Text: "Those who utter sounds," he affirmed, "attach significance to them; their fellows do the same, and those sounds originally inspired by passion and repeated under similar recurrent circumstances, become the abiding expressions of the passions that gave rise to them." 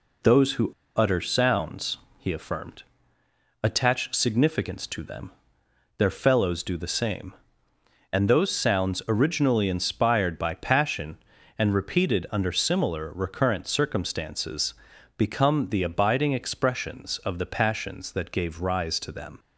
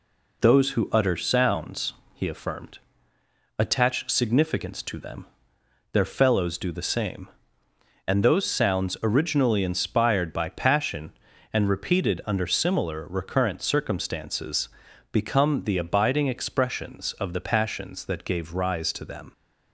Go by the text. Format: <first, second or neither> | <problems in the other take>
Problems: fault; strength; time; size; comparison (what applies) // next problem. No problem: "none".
second | pauses between "who" and "utter"; slight; at 0.7 s; 0.24 s long